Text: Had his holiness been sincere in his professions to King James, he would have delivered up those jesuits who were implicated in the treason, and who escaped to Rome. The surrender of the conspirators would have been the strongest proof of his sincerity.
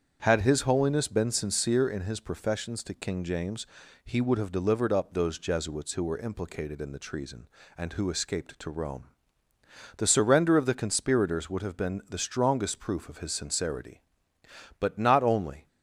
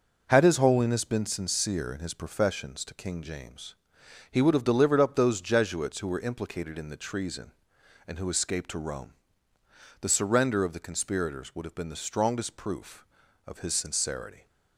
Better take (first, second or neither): second